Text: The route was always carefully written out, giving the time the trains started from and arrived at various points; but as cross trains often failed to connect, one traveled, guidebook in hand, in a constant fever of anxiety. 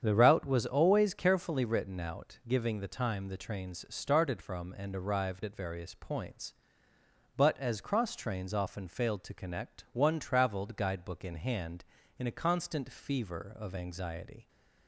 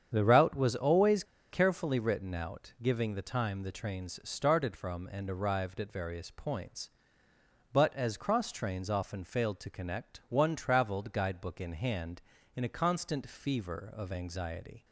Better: first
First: starts louder than the rest; strong; until 1.0 s; 8 dB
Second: starts louder than the rest; strong; until 1.1 s; 8 dB // pauses between "always" and "carefully"; slight; at 1.2 s; 0.27 s long

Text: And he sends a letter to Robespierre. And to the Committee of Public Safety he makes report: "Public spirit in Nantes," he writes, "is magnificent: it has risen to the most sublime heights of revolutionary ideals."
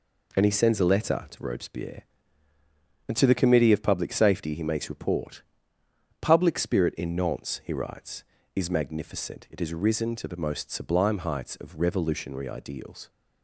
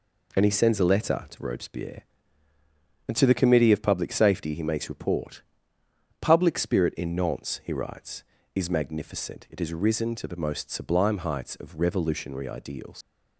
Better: first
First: none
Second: leaves "ideals" unfinished; at 13.0 s; 85 ms

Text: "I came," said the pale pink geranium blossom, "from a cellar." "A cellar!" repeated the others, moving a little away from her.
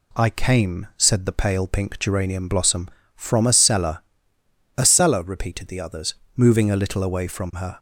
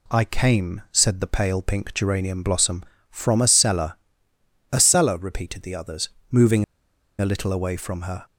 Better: first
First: none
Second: pauses between "moving" and "a"; noticeable; at 6.6 s; 0.54 s long

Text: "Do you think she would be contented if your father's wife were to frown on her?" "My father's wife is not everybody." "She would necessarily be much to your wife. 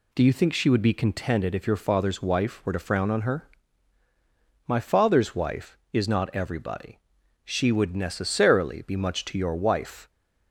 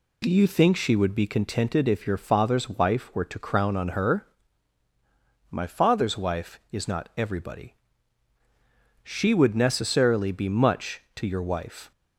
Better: first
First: none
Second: says "crown" for "frown"; at 3.3 s

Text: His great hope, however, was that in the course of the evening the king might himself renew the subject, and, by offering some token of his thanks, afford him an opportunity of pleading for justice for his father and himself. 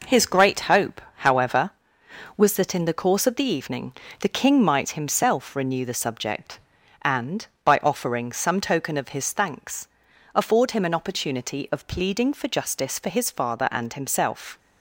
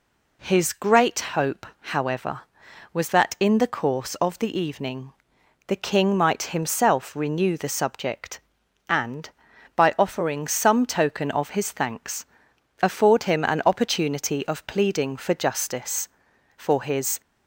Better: first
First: pauses between "evening" and "the"; slight; at 3.9 s; 0.28 s long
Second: pauses between "evening" and "the"; noticeable; at 5.1 s; 0.54 s long // stops before "father and himself"; at 17.2 s

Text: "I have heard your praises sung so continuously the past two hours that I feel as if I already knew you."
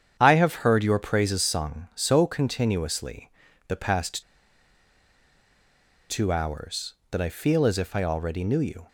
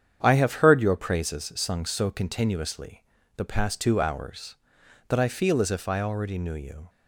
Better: second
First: starts louder than the rest; strong; until 1.2 s; 8.5 dB // pauses between "continuously" and "the"; at 3.2 s; 0.38 s long // pauses between "past" and "two"; strong; at 4.2 s; 1.8 s long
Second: starts louder than the rest; strong; until 1.2 s; 8 dB // pauses between "continuously" and "the"; at 3.0 s; 0.36 s long

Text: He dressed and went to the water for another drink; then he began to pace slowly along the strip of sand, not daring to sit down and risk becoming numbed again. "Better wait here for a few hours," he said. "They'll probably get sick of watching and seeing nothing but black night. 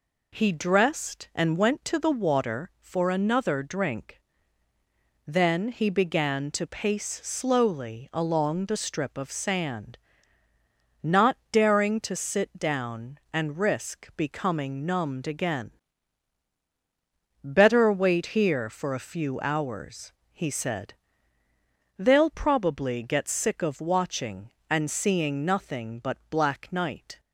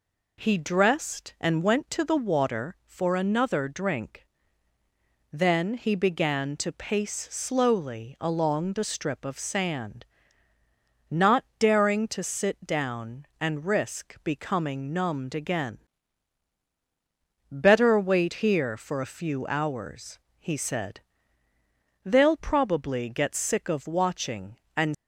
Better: first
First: pauses between "not" and "daring"; slight; at 11.3 s; 0.16 s long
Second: pauses between "not" and "daring"; slight; at 11.4 s; 0.16 s long // stops before "seeing nothing but black night"; at 24.9 s

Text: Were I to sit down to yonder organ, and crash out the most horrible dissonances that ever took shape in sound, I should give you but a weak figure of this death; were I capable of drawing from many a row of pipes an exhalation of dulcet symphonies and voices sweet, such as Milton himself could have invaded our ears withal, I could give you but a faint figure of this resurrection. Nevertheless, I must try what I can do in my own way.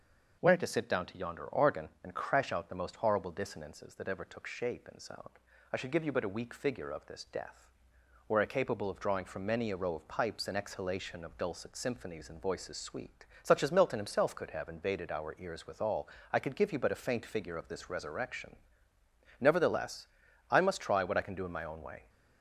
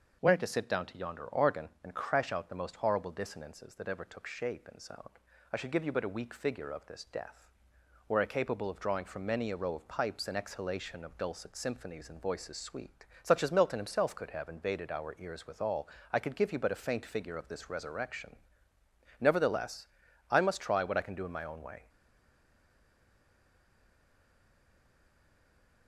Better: first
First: starts louder than the rest; noticeable; until 1.4 s; 6 dB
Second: starts louder than the rest; noticeable; until 1.2 s; 6 dB // stays silent after the last word; strong; from 21.8 s on; 4.0 s long

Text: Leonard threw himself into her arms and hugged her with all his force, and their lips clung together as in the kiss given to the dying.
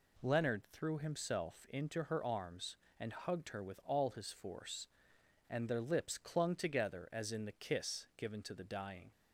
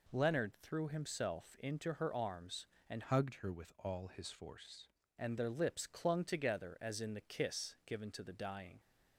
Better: first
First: none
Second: changes voice from "hugged" to "force"; from 3.0 to 4.8 s; 1.8 s long

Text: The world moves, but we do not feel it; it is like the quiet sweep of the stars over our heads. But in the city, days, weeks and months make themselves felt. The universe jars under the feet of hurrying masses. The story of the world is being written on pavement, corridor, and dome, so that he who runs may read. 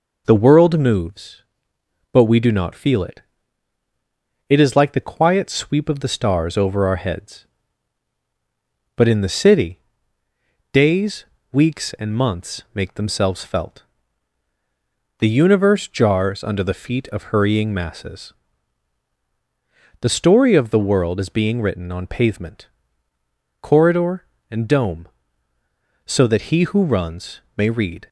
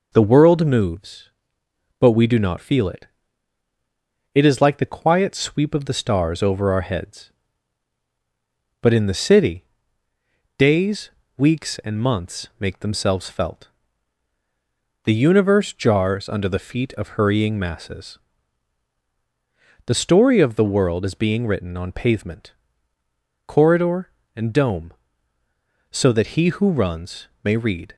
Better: neither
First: pauses between "runs" and "may"; slight; at 27.4 s; 0.16 s long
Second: pauses between "runs" and "may"; slight; at 27.2 s; 0.16 s long

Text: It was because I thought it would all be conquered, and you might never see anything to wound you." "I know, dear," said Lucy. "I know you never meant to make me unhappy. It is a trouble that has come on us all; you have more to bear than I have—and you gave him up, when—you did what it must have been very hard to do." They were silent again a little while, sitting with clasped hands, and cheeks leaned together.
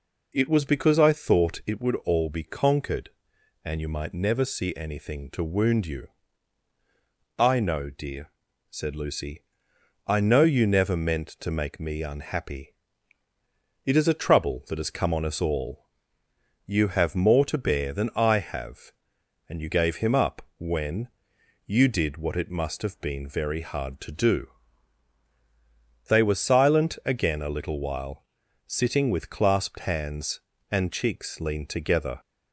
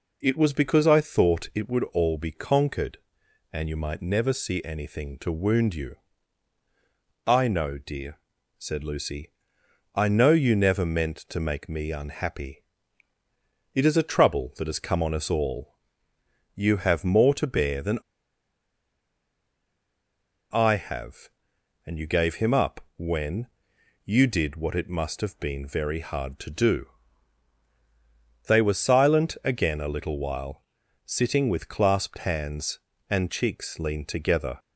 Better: first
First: none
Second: pauses between "than" and "I"; strong; at 17.9 s; 2.5 s long

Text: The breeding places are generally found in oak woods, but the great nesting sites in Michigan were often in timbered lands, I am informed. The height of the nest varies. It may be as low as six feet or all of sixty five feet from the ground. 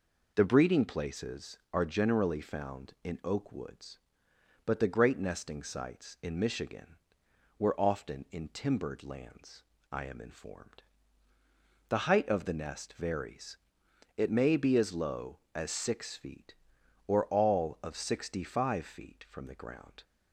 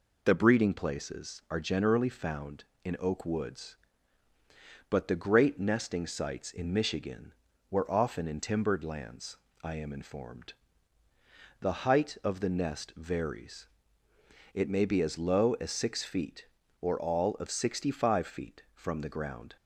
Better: neither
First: none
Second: none

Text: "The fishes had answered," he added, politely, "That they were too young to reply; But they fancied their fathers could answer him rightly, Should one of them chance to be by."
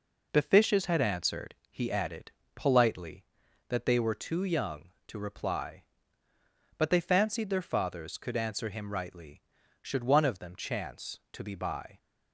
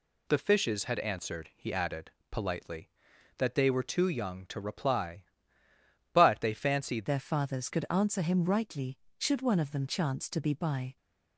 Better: first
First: none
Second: changes voice at "their"; from 7.0 s on; 3.9 s long

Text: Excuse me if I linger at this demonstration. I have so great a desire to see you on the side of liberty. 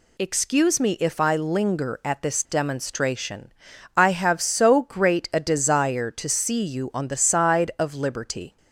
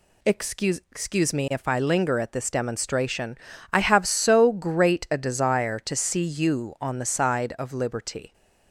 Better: first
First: none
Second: says "Excuse" twice; at 0.9 s

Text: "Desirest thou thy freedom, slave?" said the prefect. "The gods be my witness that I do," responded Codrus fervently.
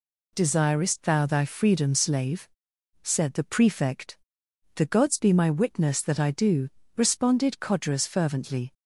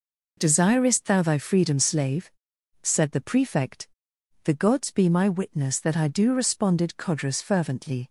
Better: neither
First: none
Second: none

